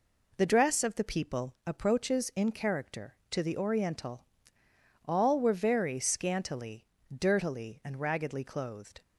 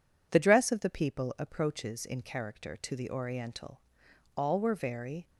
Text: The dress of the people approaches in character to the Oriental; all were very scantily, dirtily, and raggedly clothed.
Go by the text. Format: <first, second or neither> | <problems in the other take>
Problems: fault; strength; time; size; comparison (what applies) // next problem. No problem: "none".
first | stops before "scantily dirtily and raggedly clothed"; at 5.2 s